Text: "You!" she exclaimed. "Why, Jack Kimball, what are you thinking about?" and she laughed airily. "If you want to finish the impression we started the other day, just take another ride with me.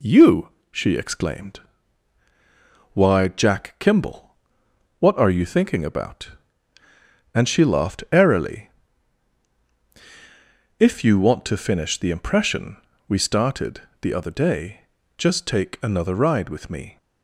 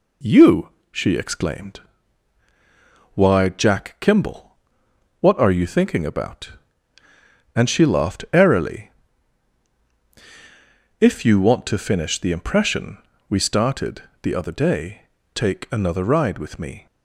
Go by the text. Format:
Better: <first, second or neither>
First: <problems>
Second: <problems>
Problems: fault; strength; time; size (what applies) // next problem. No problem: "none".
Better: first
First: pauses between "impression" and "we"; slight; at 12.7 s; 0.32 s long // pauses between "started" and "the"; slight; at 13.8 s; 0.18 s long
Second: pauses between "impression" and "we"; slight; at 12.9 s; 0.32 s long // pauses between "started" and "the"; slight; at 14.0 s; 0.18 s long // skips "just"; at 15.2 s